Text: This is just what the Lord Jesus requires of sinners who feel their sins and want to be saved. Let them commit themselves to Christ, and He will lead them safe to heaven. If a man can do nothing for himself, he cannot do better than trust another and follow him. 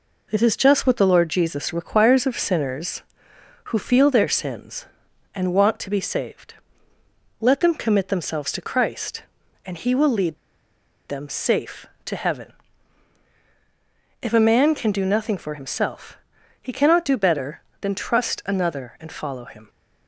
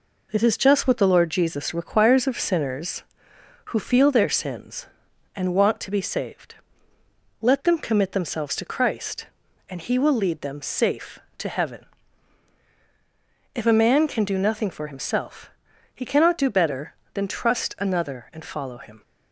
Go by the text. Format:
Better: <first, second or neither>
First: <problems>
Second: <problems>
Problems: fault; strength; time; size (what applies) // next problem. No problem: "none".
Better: second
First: pauses between "lead" and "them"; noticeable; at 10.3 s; 0.71 s long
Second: none